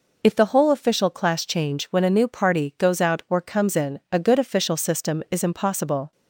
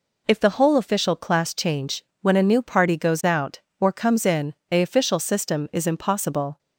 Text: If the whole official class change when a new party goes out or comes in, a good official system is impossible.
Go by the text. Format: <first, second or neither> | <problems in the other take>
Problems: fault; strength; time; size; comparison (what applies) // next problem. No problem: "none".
first | pauses between "change" and "when"; slight; at 2.0 s; 0.20 s long // skips "good"; at 4.8 s